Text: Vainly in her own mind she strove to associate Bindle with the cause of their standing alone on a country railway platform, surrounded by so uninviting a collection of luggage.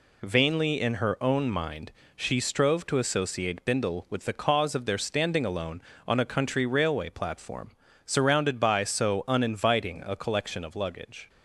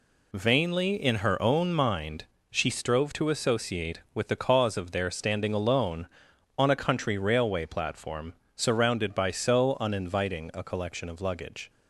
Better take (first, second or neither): first